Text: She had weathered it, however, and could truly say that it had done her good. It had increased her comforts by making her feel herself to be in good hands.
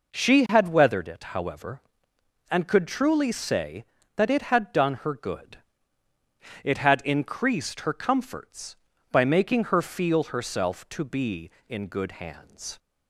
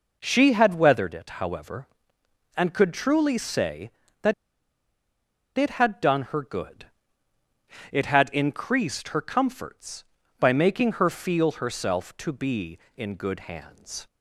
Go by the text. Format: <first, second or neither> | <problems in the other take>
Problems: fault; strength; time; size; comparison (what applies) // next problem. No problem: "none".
first | pauses between "that" and "it"; at 4.3 s; 1.2 s long